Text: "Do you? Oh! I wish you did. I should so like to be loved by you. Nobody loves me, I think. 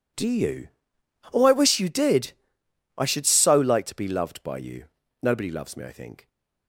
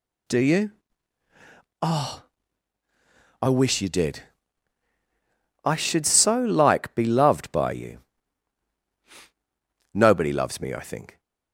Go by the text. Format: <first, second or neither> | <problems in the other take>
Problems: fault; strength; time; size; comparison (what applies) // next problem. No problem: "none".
first | skips "to"; at 6.9 s